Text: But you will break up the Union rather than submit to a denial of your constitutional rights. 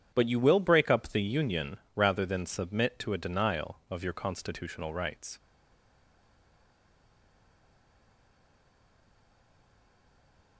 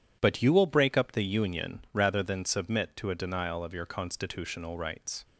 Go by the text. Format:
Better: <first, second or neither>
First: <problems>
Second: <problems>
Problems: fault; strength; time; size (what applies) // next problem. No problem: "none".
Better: second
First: pauses between "Union" and "rather"; slight; at 1.7 s; 0.18 s long // stays silent after the last word; strong; from 5.3 s on; 5.2 s long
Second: none